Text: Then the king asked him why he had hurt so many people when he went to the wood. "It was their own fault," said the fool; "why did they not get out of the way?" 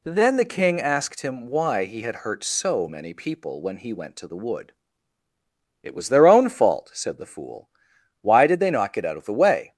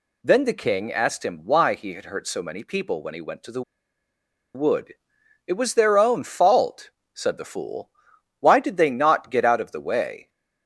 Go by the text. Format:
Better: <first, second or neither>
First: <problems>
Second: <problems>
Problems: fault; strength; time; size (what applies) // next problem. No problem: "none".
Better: first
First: none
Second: pauses between "the" and "wood"; noticeable; at 3.6 s; 0.93 s long